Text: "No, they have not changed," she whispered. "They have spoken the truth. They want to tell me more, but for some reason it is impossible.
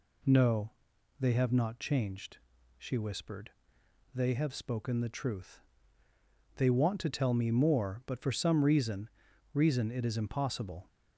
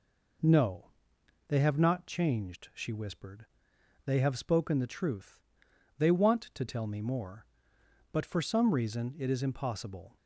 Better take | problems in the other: second | says "reason" twice; at 9.5 s

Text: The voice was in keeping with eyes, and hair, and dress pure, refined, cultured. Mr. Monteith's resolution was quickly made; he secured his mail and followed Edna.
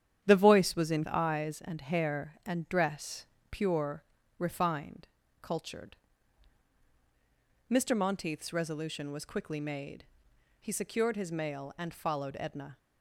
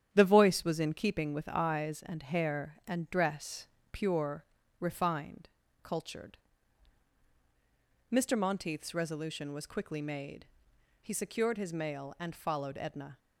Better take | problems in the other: second | starts louder than the rest; strong; until 1.2 s; 9.5 dB; strong in the second // skips "keeping with"; at 1.0 s // pauses between "dress" and "pure"; slight; at 3.2 s; 0.26 s long; slight in the second

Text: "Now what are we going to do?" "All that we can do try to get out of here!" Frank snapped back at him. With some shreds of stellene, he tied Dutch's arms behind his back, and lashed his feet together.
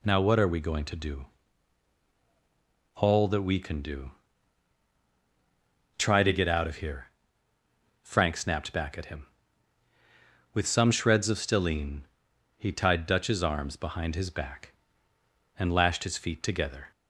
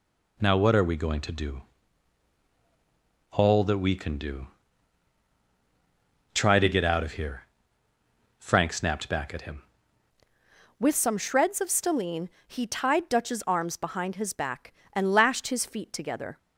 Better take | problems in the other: first | pauses between "do" and "try"; strong; at 4.4 s; 1.8 s long; strong in the first // changes voice at "With"; from 10.7 s on; 5.6 s long

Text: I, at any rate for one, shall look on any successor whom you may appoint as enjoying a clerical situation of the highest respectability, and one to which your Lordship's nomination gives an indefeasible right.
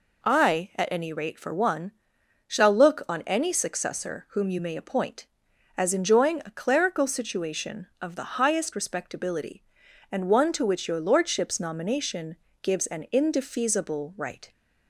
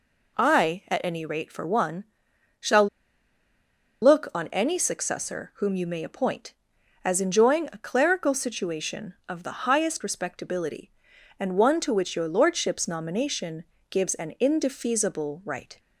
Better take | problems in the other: first | pauses between "shall" and "look"; at 2.8 s; 1.1 s long // pauses between "nomination" and "gives"; slight; at 13.6 s; 0.28 s long; slight in the first

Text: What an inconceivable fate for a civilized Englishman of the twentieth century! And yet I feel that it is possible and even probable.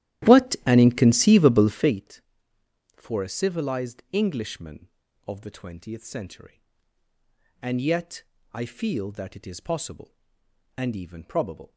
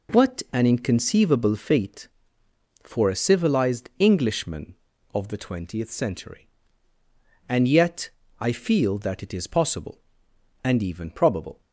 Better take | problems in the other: second | starts louder than the rest; strong; until 2.1 s; 13 dB // pauses between "yet" and "I"; slight; at 8.2 s; 0.30 s long; slight in the second

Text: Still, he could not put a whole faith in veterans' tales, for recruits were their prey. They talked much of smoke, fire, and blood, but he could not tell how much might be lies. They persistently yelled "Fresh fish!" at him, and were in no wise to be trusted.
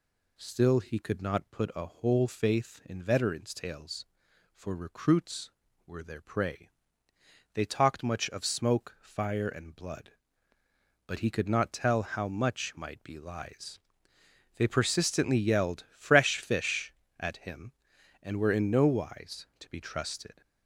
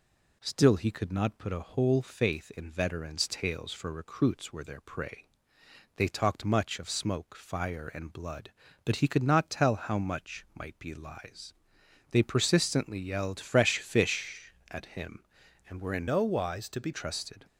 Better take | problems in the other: first | changes voice from "no" to "be"; from 16.0 to 16.9 s; 0.9 s long

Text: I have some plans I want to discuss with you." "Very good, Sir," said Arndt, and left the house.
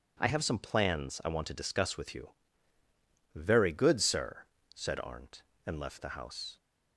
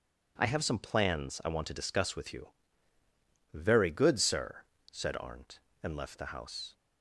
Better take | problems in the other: neither | none

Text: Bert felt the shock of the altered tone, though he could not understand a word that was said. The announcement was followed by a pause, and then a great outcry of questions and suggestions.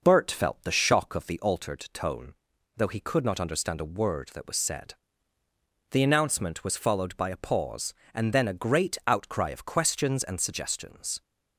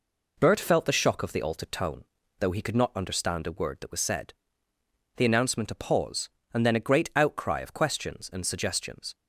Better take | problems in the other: first | skips "was followed by"; at 5.7 s

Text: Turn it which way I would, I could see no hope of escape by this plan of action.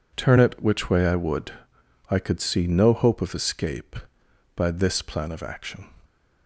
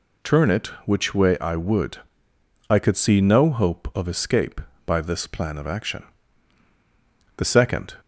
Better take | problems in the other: first | goes on to say "The second"; from 7.3 s on; 0.58 s long

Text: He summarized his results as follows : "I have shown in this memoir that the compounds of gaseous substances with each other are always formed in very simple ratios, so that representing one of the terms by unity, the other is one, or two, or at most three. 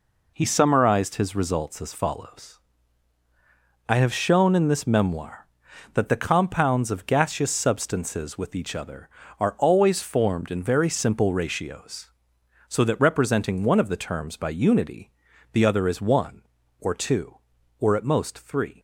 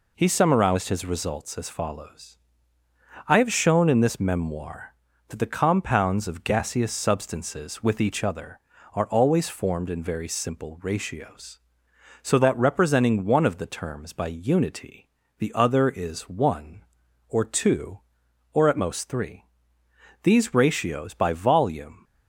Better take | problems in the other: first | goes on to say "These ratios by volume"; strong; from 20.2 s on; 1.8 s long

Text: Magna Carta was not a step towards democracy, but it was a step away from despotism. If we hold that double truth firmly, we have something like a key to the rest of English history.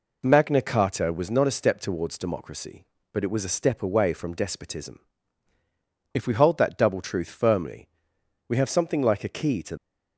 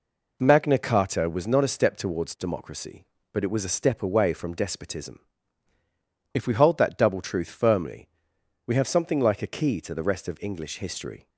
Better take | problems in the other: second | stops before "the rest of English history"; at 9.7 s

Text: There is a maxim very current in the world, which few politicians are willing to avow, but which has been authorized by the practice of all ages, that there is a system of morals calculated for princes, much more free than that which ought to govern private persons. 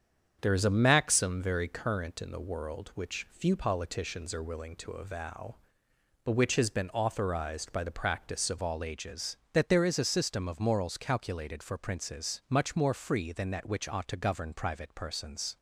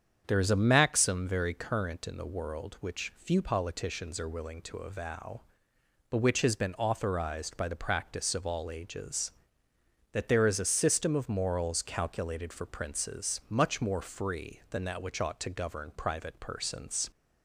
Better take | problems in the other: second | starts louder than the rest; strong; until 1.4 s; 7.5 dB; strong in the second // changes voice at "all"; from 8.6 s on; 6.9 s long

